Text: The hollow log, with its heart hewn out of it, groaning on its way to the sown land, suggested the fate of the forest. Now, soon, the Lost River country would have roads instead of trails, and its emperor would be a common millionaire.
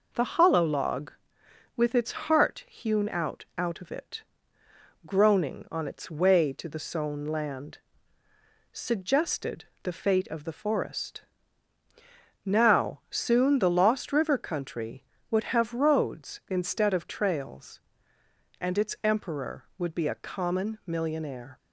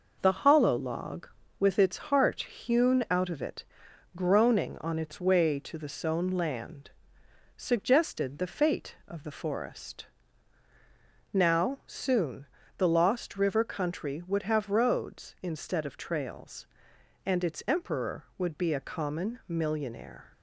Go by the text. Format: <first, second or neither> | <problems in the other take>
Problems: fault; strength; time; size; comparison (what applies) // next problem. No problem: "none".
second | says "out" twice; at 3.5 s // pauses between "suggested" and "the"; slight; at 9.6 s; 0.20 s long